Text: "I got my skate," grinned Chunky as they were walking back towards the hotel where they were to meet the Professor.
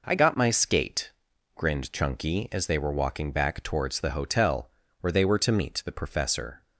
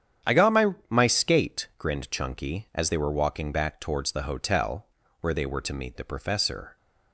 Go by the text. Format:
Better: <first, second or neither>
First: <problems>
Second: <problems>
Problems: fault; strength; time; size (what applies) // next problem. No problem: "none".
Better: first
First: pauses between "hotel" and "where"; slight; at 4.6 s; 0.30 s long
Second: starts louder than the rest; strong; until 1.3 s; 9 dB // says "my" twice; at 0.8 s // pauses between "hotel" and "where"; slight; at 4.8 s; 0.36 s long